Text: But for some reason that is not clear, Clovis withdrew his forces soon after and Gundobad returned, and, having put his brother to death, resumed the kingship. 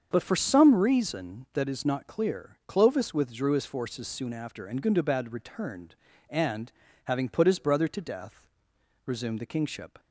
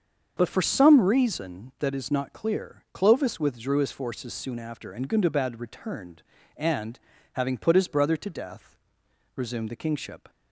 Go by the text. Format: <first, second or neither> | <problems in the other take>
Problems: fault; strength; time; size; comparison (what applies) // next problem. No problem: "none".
neither | starts louder than the rest; the same in both